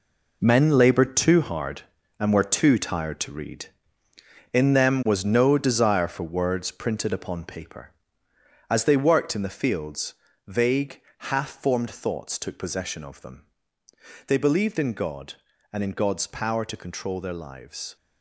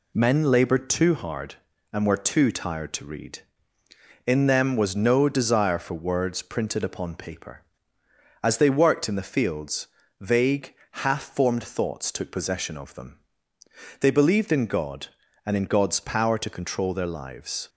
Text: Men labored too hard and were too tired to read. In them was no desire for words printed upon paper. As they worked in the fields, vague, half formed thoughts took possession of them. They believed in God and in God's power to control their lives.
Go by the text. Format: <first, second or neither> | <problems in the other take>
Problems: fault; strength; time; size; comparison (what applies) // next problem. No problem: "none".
second | gets quieter; strong; throughout; 10 dB